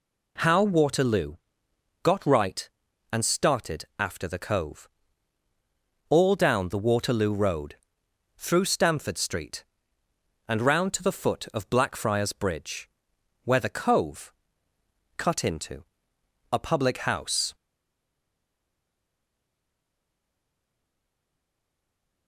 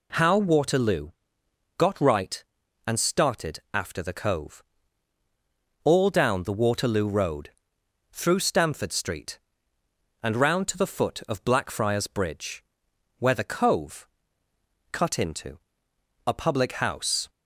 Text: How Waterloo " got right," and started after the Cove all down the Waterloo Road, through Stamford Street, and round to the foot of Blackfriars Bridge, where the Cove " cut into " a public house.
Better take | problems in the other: second | pauses between "Cove" and "all"; at 4.8 s; 1.2 s long; also in the second // stays silent after the last word; strong; from 17.5 s on; 4.7 s long

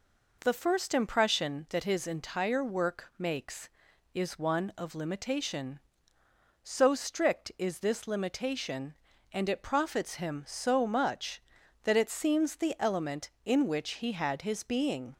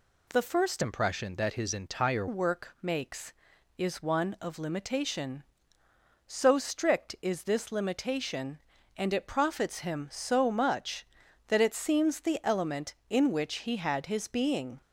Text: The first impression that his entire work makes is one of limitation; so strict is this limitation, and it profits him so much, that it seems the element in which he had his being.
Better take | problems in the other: first | changes voice from "impression" to "entire"; from 0.8 to 2.2 s; 1.4 s long

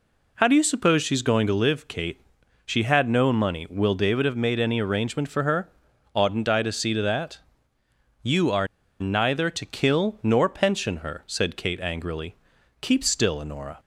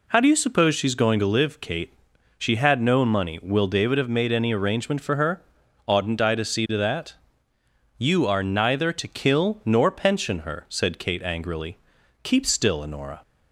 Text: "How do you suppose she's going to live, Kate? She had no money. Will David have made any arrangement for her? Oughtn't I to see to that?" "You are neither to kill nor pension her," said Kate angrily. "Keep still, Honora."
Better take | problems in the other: second | pauses between "are" and "neither"; slight; at 8.6 s; 0.33 s long

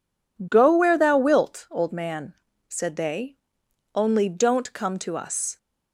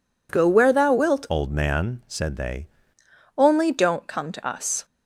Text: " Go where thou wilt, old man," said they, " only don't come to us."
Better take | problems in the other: first | changes voice from "old" to "they"; from 1.2 to 2.6 s; 1.4 s long

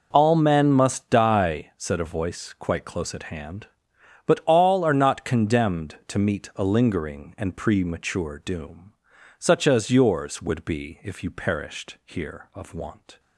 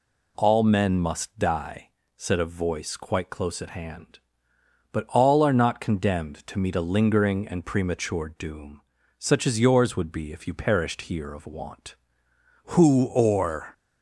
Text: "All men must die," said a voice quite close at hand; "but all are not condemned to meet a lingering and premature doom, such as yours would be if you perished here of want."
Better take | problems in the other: first | goes on to say "Who or"; noticeable; from 12.7 s on; 1.0 s long

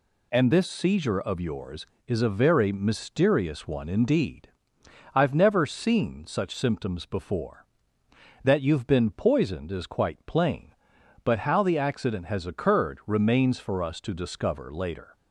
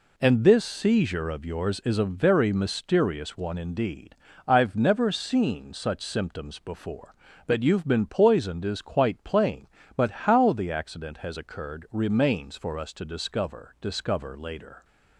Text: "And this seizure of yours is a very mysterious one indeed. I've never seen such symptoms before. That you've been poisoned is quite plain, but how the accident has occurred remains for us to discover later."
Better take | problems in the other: first | says "discover" twice; at 13.8 s

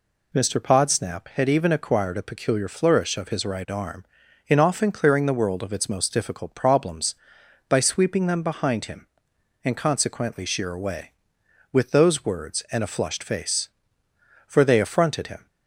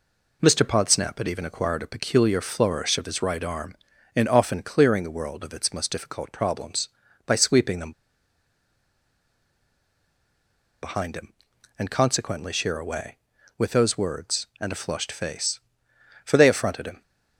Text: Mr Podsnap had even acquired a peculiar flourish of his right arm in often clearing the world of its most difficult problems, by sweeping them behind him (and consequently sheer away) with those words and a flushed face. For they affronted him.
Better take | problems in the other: first | pauses between "them" and "behind"; strong; at 7.9 s; 2.9 s long

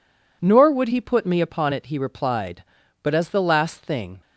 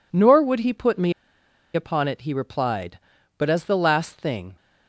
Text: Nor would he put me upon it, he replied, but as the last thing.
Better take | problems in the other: first | pauses between "me" and "upon"; noticeable; at 1.1 s; 0.62 s long

